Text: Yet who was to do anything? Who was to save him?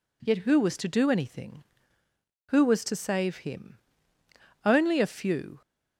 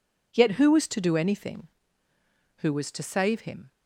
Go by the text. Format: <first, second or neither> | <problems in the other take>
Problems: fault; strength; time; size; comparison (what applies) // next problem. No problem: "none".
second | goes on to say "Only a few"; noticeable; from 4.6 s on; 0.98 s long